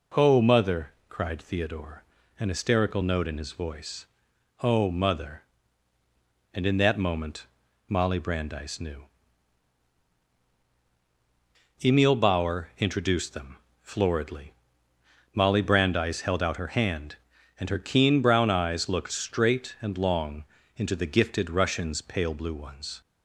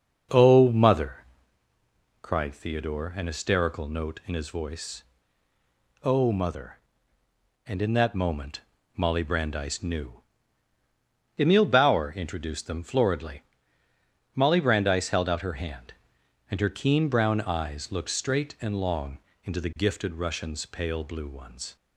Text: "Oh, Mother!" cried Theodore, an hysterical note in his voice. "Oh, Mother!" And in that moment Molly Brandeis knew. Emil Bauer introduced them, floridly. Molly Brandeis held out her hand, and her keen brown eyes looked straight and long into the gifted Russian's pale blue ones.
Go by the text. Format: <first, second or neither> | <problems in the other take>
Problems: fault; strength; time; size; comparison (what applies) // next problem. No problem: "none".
first | starts louder than the rest; until 1.5 s; 6.5 dB // pauses between "moment" and "Molly"; slight; at 8.6 s; 0.34 s long; also in the first // pauses between "long" and "into"; slight; at 19.1 s; 0.26 s long; slight in the first